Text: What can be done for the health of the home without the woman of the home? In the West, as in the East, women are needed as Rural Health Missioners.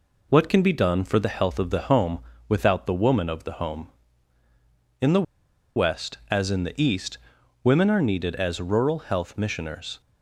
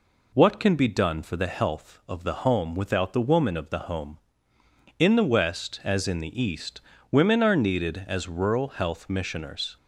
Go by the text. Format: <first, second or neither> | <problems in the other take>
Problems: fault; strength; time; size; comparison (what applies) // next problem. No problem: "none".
second | pauses between "home" and "without"; slight; at 2.1 s; 0.28 s long // pauses between "the" and "West"; noticeable; at 5.2 s; 0.53 s long